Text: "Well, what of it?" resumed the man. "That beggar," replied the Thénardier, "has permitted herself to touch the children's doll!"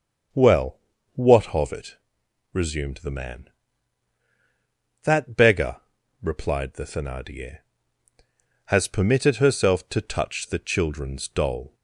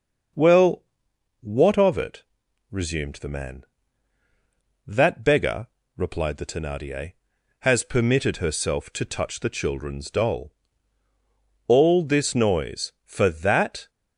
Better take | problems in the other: first | starts louder than the rest; until 1.9 s; 6 dB; also in the first // goes on to say "All this noise for that"; strong; from 11.6 s on; 2.2 s long

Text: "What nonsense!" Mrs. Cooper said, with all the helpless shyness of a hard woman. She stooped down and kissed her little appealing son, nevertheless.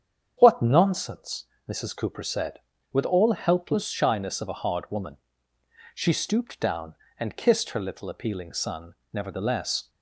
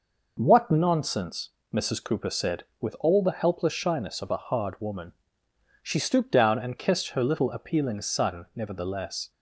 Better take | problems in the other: second | starts louder than the rest; strong; until 1.4 s; 8 dB // skips "the"; at 3.3 s

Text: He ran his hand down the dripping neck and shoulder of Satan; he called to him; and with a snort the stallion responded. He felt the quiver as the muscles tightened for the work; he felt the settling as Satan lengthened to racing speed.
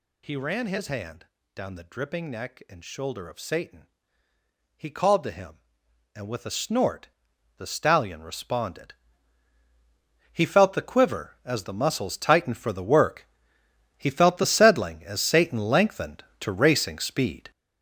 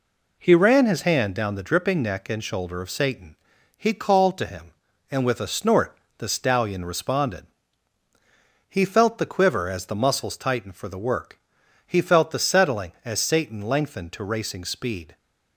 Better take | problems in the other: second | gets louder; strong; throughout; 8.5 dB // pauses between "hand" and "down"; slight; at 1.2 s; 0.28 s long // pauses between "snort" and "the"; noticeable; at 7.0 s; 0.50 s long; slight in the second

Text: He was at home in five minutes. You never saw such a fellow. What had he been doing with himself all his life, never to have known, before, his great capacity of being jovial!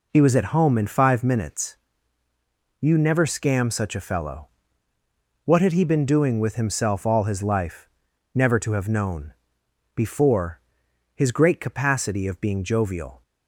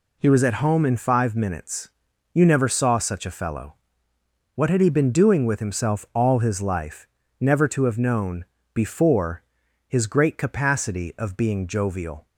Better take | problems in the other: second | says "scam" for "saw"; at 3.2 s

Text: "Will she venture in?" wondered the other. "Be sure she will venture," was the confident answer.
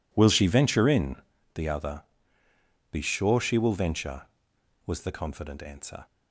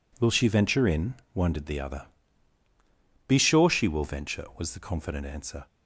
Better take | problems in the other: second | skips "wondered"; at 1.3 s

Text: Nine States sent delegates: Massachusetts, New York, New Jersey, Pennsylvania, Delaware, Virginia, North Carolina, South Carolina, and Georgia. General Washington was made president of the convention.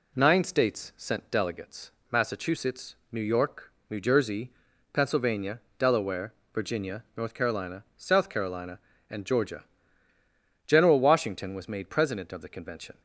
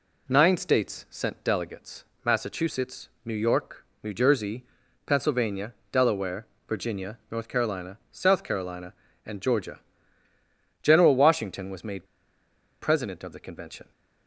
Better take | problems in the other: first | pauses between "made" and "president"; noticeable; at 12.0 s; 0.77 s long

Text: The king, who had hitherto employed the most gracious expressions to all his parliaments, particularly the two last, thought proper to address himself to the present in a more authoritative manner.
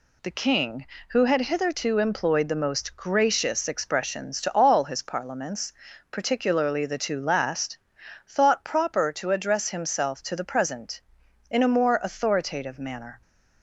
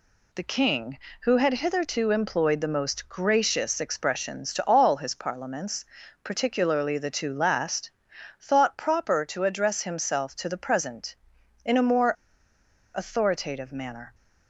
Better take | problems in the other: first | pauses between "more" and "authoritative"; noticeable; at 12.1 s; 0.81 s long

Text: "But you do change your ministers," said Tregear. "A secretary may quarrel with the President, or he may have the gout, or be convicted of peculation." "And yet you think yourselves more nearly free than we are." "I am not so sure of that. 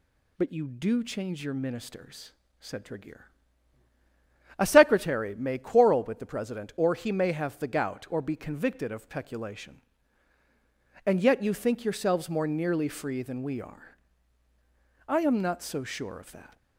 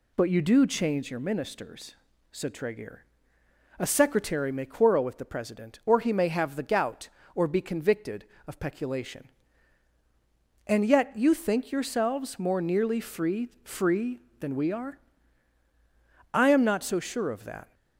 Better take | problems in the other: first | says "free" twice; at 13.6 s

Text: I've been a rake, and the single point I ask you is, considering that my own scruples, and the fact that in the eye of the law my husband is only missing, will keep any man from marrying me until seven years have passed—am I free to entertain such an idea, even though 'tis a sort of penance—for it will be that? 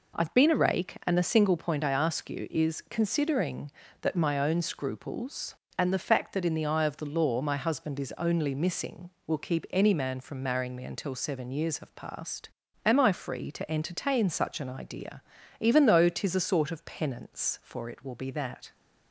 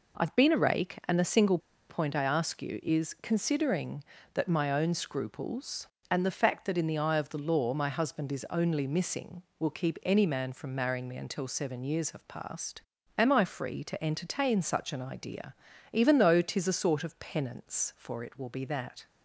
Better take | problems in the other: first | pauses between "single" and "point"; slight; at 1.5 s; 0.31 s long

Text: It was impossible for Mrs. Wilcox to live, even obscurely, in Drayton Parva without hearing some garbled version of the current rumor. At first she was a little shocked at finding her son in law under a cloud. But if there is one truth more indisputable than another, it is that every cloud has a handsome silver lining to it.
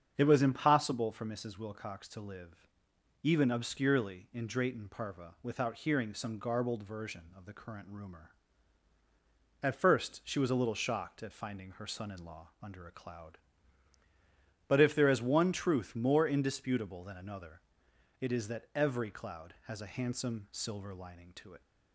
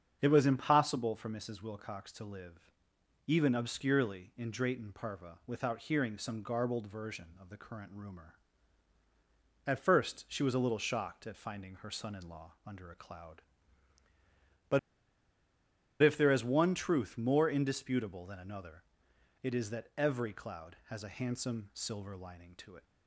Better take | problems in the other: first | starts louder than the rest; strong; until 1.2 s; 7.5 dB; strong in the first // pauses between "But" and "if"; at 14.7 s; 1.2 s long

